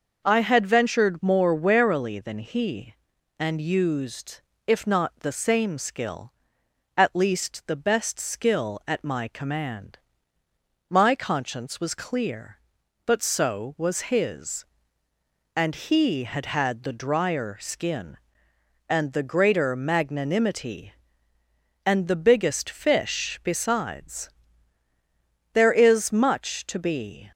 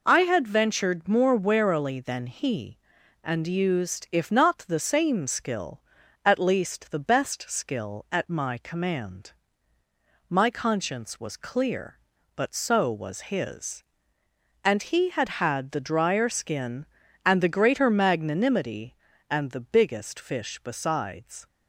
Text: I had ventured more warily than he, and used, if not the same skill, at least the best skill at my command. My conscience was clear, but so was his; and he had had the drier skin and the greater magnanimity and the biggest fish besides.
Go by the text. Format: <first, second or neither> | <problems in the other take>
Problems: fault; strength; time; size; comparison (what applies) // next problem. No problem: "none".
second | goes on to say "There is much to be"; strong; from 25.5 s on; 1.7 s long